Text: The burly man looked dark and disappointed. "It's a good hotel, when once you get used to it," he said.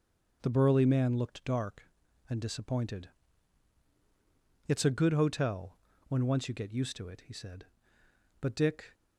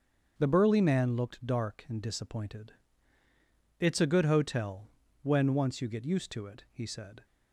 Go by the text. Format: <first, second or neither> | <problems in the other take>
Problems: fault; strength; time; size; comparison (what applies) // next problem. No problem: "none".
second | starts louder than the rest; until 1.4 s; 6.5 dB; also in the second // goes on to say "But Dick"; from 8.3 s on; 0.56 s long